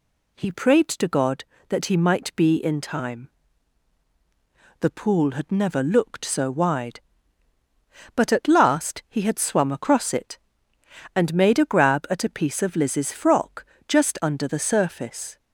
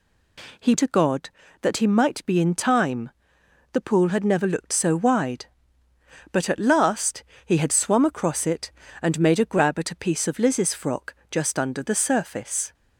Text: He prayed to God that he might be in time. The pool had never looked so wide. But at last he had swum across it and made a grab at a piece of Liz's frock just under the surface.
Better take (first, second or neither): first